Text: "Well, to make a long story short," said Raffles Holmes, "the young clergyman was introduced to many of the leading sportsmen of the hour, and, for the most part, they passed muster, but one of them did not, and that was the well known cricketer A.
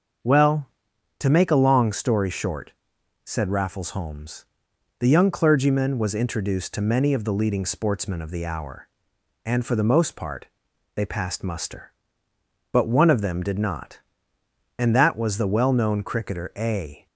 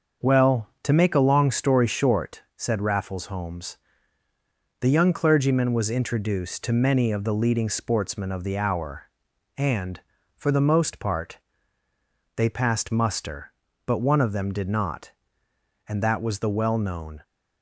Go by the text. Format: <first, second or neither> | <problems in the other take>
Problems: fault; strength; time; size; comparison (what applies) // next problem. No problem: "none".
first | starts louder than the rest; until 1.3 s; 6.5 dB; also in the first // stops before "cricketer A"; at 17.2 s